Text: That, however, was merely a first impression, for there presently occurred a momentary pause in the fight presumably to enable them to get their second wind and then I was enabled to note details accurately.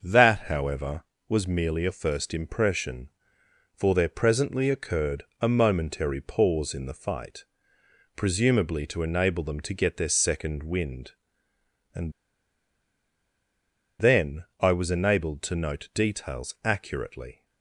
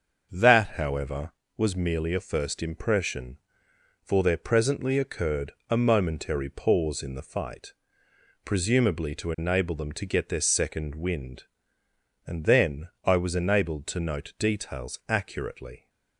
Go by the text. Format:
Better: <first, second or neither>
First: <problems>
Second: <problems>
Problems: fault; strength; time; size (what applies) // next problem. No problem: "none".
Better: second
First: starts louder than the rest; until 1.0 s; 6.5 dB // pauses between "occurred" and "a"; slight; at 5.2 s; 0.18 s long // pauses between "fight" and "presumably"; noticeable; at 7.4 s; 0.70 s long // pauses between "and" and "then"; strong; at 12.1 s; 1.8 s long // pauses between "then" and "I"; slight; at 14.4 s; 0.16 s long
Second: starts louder than the rest; until 1.3 s; 6.5 dB // pauses between "occurred" and "a"; slight; at 5.5 s; 0.18 s long // pauses between "fight" and "presumably"; noticeable; at 7.7 s; 0.70 s long // pauses between "then" and "I"; slight; at 12.8 s; 0.16 s long